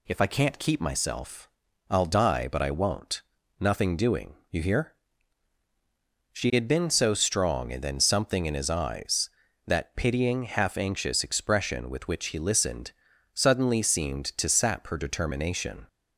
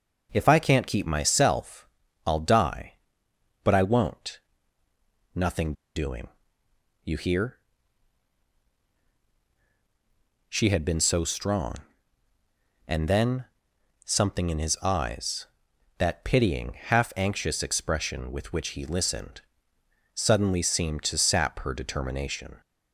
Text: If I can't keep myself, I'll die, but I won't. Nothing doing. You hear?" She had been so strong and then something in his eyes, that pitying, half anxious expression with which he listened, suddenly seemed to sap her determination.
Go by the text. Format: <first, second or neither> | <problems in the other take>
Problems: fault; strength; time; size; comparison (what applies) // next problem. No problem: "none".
first | pauses between "Nothing" and "doing"; slight; at 5.7 s; 0.22 s long // pauses between "then" and "something"; noticeable; at 13.4 s; 0.60 s long